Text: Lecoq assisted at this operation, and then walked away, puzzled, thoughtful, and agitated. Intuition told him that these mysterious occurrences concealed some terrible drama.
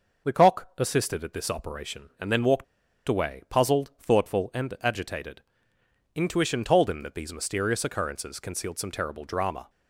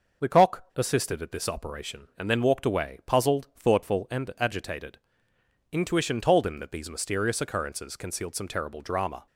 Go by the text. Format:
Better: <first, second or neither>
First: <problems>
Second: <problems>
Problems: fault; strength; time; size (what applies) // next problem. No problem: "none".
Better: second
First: pauses between "walked" and "away"; at 2.6 s; 0.44 s long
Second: none